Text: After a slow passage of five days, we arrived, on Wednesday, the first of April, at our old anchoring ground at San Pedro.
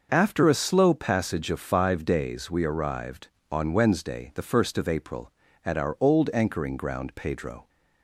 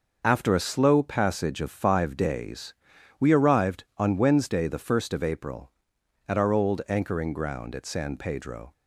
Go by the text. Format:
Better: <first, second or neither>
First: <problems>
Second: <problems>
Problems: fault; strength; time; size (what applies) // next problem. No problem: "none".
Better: second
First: starts louder than the rest; noticeable; until 1.1 s; 6 dB // skips "at San"; at 7.1 s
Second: none